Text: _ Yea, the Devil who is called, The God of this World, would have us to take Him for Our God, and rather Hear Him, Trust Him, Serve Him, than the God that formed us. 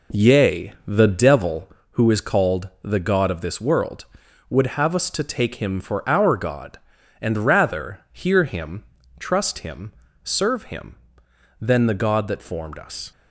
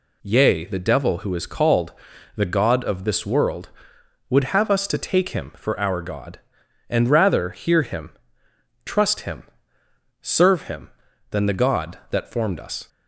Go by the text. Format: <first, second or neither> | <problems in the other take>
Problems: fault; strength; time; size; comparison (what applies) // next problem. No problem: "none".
second | starts louder than the rest; until 1.8 s; 3.5 dB